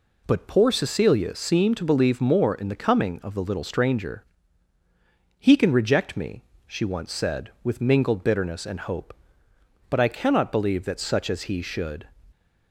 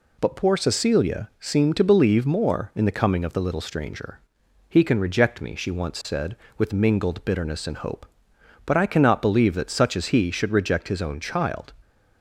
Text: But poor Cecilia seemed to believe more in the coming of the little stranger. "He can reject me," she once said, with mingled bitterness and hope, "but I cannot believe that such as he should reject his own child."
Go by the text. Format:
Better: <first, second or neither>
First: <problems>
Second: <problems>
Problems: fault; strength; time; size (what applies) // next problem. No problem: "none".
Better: second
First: stops before "reject his own child"; at 12.3 s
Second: none